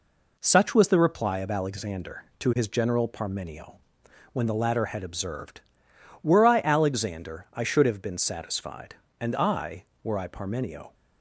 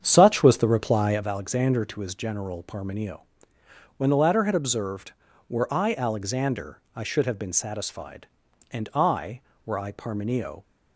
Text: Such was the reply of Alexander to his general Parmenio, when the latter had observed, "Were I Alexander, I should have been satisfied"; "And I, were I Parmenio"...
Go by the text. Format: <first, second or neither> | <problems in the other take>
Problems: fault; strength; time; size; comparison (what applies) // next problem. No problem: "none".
first | starts louder than the rest; strong; until 1.3 s; 8 dB